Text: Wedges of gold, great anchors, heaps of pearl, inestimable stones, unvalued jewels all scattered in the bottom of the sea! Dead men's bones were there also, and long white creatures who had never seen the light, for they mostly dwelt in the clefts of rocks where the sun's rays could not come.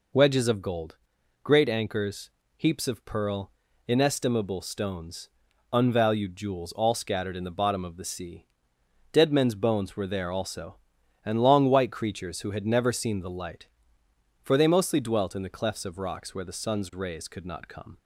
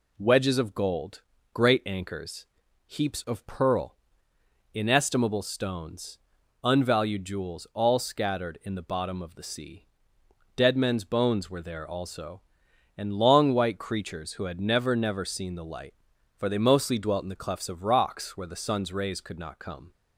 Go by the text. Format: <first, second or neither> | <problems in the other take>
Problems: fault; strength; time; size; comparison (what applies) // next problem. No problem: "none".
first | says "never" twice; at 14.9 s